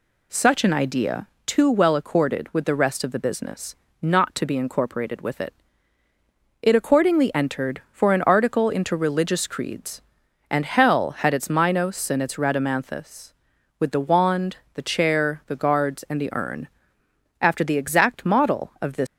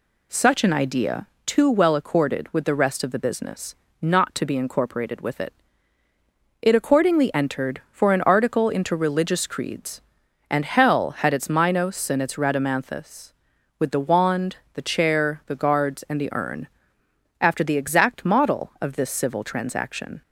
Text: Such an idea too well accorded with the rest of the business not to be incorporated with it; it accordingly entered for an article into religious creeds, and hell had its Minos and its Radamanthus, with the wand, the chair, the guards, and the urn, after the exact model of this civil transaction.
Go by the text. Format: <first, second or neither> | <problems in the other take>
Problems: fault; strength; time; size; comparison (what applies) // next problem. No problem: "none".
second | pauses between "idea" and "too"; slight; at 1.2 s; 0.22 s long; slight in the second // pauses between "business" and "not"; slight; at 3.7 s; 0.26 s long; slight in the second // stops before "civil transaction"; at 19.0 s